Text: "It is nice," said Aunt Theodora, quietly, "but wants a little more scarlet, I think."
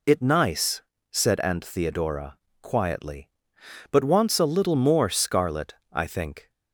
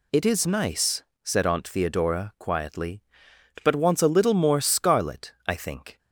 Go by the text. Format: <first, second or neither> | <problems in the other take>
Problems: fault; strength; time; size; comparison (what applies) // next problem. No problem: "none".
second | skips "is"; at 0.2 s